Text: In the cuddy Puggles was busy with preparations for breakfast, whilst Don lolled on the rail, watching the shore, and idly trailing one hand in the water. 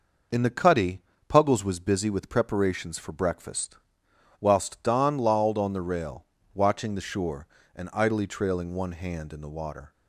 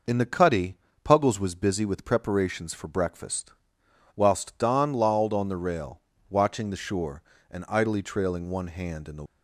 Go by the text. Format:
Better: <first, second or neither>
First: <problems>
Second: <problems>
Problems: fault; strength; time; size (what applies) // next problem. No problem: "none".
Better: first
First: pauses between "cuddy" and "Puggles"; slight; at 1.0 s; 0.28 s long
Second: pauses between "cuddy" and "Puggles"; slight; at 0.7 s; 0.28 s long // stops before "water"; at 9.2 s